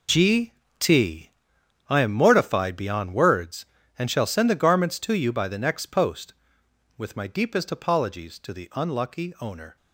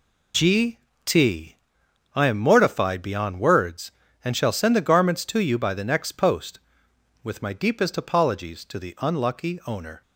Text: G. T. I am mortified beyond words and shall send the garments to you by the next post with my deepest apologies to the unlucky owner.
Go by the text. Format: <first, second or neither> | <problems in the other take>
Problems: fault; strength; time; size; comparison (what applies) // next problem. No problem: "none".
second | gets quieter; strong; throughout; 12.5 dB // pauses between "G" and "T"; slight; at 0.5 s; 0.26 s long; slight in the second // pauses between "T" and "I"; noticeable; at 1.2 s; 0.58 s long; noticeable in the second